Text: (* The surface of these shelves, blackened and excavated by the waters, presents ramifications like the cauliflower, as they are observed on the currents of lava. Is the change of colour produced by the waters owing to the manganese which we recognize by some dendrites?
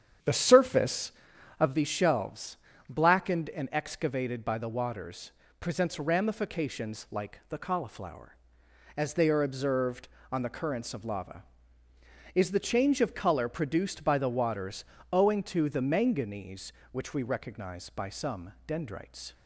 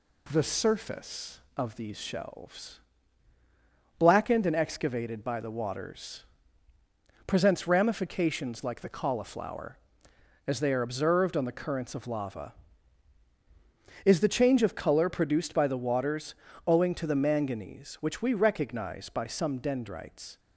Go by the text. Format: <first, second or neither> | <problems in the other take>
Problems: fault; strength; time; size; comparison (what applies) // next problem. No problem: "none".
second | starts louder than the rest; strong; until 1.8 s; 8.5 dB // pauses between "waters" and "owing"; slight; at 14.8 s; 0.26 s long; slight in the second